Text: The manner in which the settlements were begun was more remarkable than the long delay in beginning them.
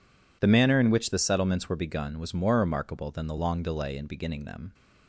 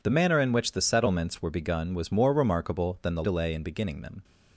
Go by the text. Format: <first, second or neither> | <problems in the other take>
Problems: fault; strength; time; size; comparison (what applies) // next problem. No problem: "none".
first | skips "long"; at 3.2 s